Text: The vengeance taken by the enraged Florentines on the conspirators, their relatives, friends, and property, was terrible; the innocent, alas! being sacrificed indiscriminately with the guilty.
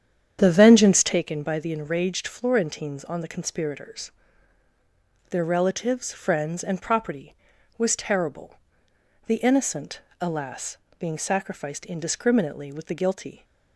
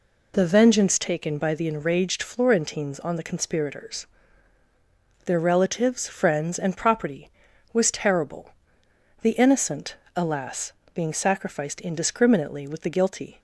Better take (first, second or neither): second